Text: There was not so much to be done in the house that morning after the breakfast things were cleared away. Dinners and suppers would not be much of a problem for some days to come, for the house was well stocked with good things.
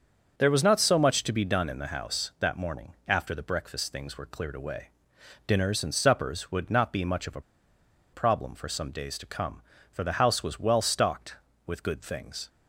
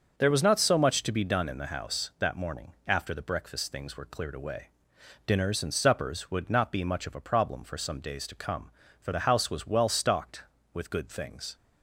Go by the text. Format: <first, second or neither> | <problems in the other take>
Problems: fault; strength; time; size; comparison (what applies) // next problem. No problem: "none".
second | starts louder than the rest; until 1.4 s; 6.5 dB; noticeable in the second // pauses between "a" and "problem"; noticeable; at 7.4 s; 0.71 s long